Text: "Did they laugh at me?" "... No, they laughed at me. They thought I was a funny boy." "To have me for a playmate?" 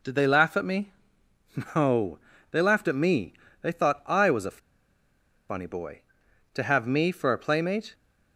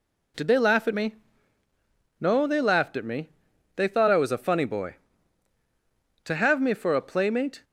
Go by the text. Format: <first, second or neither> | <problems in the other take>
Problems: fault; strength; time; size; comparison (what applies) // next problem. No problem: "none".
second | pauses between "a" and "funny"; noticeable; at 4.5 s; 0.92 s long